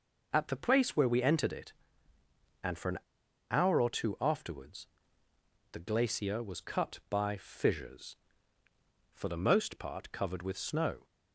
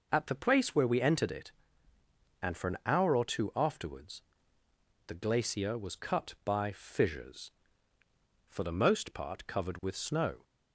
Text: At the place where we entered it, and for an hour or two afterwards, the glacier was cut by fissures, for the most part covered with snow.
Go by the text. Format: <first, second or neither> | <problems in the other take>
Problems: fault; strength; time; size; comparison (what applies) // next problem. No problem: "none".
second | pauses between "an" and "hour"; noticeable; at 2.9 s; 0.51 s long